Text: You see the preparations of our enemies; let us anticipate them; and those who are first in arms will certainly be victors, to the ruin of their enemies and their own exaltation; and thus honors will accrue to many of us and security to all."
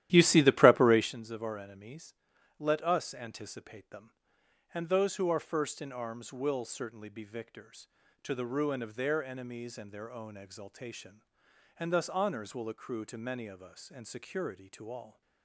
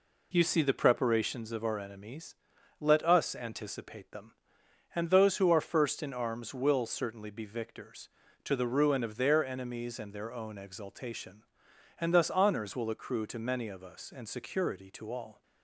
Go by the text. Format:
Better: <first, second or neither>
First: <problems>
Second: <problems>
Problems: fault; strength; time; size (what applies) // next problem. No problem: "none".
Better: second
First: starts louder than the rest; strong; until 1.1 s; 13 dB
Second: none